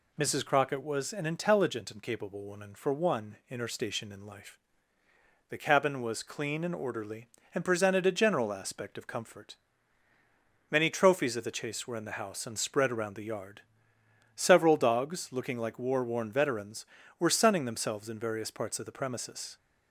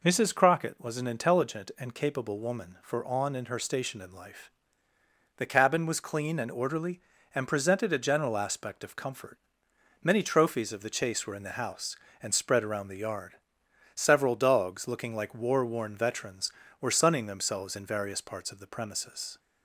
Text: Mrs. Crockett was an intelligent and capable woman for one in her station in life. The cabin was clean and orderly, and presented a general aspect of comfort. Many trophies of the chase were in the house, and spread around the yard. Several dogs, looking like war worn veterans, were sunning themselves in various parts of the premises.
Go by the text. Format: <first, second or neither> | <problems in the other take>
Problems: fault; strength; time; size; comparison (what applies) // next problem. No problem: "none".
first | says "on" for "one"; at 3.0 s